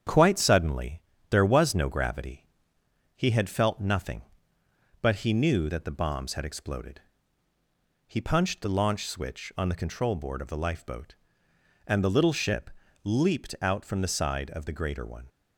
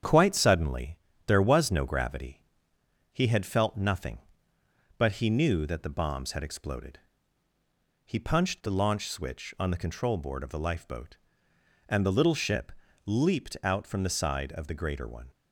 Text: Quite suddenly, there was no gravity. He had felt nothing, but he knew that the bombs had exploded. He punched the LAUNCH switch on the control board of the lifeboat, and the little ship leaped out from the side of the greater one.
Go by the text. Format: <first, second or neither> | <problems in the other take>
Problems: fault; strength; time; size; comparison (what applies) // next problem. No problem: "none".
neither | starts louder than the rest; strong; the same in both // pauses between "ship" and "leaped"; slight; the same in both